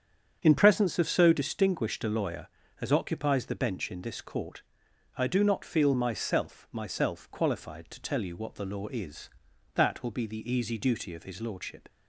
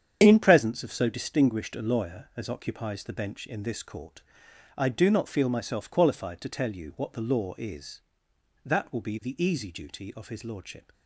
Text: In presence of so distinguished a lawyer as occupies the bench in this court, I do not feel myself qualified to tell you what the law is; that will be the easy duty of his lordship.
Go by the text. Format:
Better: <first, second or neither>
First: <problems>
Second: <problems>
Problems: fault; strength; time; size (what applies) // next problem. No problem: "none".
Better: second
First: starts louder than the rest; strong; until 1.4 s; 7.5 dB // says "myself" twice; at 6.7 s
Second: starts louder than the rest; strong; until 1.2 s; 8 dB